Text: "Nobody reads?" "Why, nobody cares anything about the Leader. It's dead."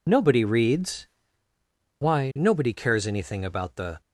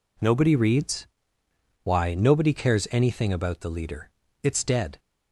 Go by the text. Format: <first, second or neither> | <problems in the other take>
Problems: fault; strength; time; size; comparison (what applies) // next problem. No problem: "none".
second | stops before "Leader It's dead"; at 4.0 s